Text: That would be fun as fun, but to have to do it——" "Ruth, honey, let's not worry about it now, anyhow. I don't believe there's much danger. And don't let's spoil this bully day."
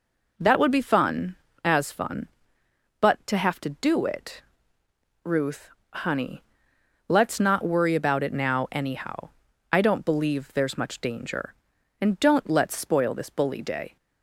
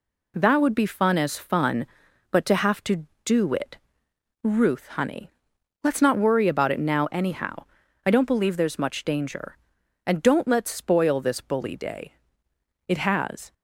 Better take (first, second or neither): first